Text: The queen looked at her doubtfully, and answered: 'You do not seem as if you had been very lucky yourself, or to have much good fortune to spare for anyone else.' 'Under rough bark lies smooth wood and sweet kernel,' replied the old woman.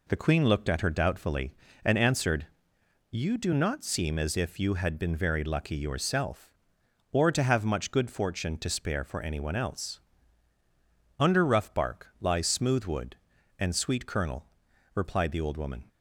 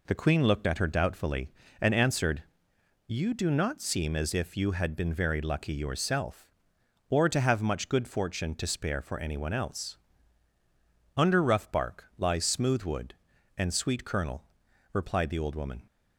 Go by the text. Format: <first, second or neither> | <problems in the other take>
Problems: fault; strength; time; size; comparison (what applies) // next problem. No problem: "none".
neither | none